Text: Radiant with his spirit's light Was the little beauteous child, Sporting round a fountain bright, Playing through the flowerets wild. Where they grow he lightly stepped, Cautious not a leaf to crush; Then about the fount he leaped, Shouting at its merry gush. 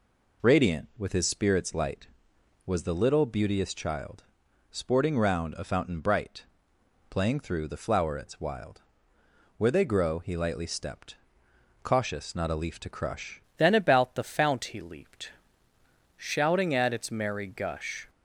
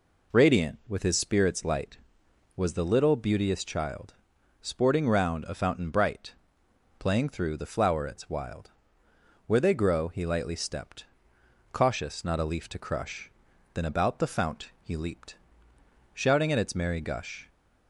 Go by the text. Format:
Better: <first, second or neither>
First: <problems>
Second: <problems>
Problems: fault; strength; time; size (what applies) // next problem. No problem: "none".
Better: second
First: changes voice at "Then"; from 13.5 s on; 4.5 s long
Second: none